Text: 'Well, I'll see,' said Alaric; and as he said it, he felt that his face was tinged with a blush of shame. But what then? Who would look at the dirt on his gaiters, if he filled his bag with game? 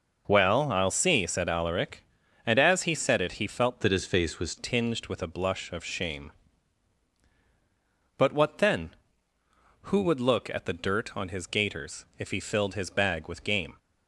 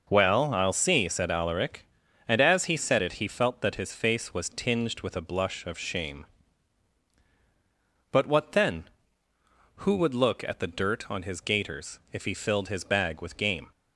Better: second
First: changes voice from "that" to "was"; from 3.8 to 4.5 s; 0.7 s long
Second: none

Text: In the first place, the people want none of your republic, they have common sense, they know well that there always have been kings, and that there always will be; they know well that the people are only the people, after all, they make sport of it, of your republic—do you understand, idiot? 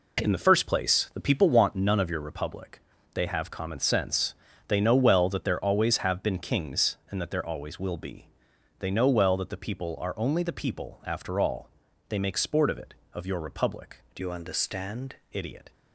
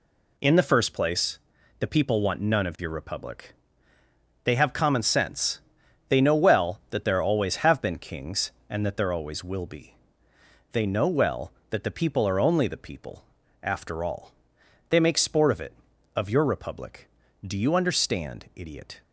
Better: second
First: changes voice from "you" to "understand"; from 14.2 to 15.1 s; 0.9 s long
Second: none

